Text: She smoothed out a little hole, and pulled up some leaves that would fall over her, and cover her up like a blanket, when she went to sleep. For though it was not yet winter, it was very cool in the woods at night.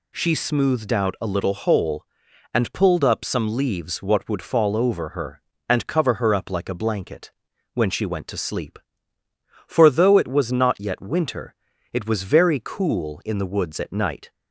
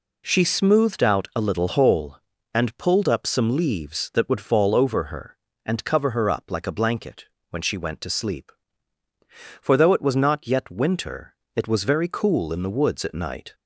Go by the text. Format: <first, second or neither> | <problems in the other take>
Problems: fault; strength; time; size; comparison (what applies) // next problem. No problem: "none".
second | says "what" for "that"; at 3.9 s